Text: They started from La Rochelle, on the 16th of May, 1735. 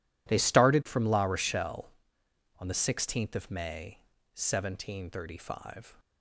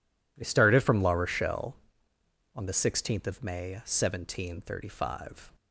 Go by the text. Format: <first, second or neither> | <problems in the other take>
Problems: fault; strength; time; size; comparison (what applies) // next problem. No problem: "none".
neither | none